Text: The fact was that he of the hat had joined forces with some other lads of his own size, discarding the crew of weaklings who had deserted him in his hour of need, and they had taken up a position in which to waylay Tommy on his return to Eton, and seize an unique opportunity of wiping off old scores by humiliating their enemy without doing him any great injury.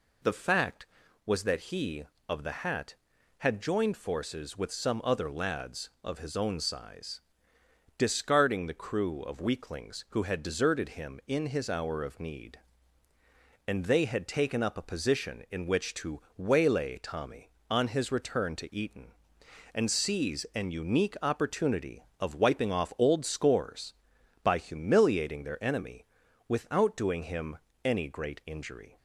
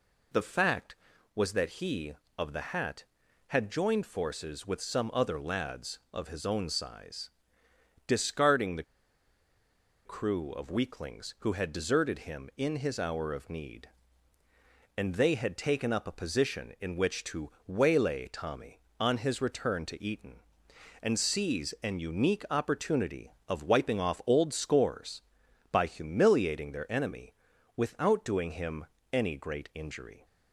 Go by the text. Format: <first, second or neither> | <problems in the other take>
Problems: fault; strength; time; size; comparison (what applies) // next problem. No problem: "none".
first | pauses between "the" and "crew"; at 8.8 s; 1.2 s long // pauses between "to" and "waylay"; slight; at 17.5 s; 0.16 s long; slight in the first // pauses between "enemy" and "without"; at 27.3 s; 0.42 s long; also in the first // pauses between "him" and "any"; slight; at 28.8 s; 0.28 s long; slight in the first